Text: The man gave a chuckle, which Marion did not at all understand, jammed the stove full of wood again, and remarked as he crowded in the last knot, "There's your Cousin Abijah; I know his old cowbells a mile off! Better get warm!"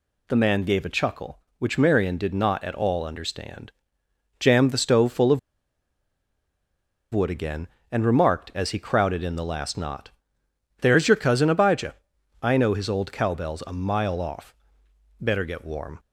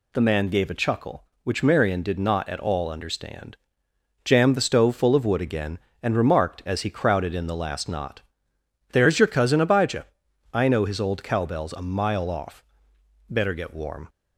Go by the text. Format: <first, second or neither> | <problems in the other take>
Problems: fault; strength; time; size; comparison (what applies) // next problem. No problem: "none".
second | pauses between "of" and "wood"; strong; at 5.3 s; 1.7 s long